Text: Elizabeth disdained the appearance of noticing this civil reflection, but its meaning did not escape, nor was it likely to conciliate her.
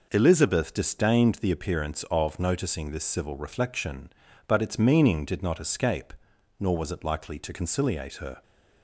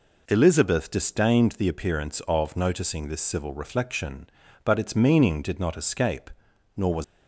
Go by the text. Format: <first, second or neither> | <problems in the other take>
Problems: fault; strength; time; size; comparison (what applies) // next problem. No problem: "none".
first | stops before "it likely to conciliate her"; at 7.0 s